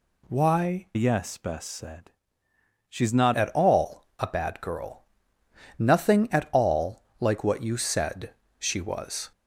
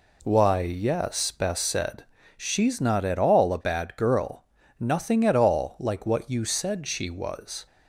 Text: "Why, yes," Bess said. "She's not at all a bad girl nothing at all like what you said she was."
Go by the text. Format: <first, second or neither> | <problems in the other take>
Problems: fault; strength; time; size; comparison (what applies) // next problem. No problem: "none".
second | changes voice from "yes" to "not"; from 0.9 to 3.3 s; 2.4 s long // pauses between "girl" and "nothing"; noticeable; at 5.0 s; 0.74 s long; slight in the second // pauses between "all" and "like"; slight; at 7.0 s; 0.18 s long // pauses between "said" and "she"; slight; at 8.3 s; 0.24 s long